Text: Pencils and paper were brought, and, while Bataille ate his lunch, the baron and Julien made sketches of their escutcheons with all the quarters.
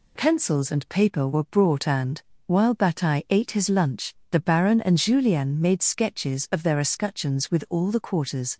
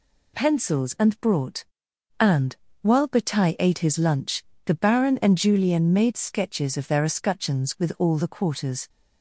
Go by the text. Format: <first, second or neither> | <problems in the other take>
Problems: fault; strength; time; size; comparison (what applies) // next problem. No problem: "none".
first | skips "paper were"; at 1.1 s